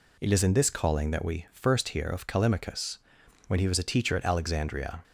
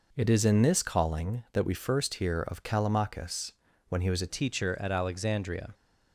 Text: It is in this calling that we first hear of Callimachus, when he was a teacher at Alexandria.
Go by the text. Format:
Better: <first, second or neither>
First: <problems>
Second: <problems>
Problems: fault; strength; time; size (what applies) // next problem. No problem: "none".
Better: first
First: none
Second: changes voice at "teacher"; from 4.2 s on; 1.5 s long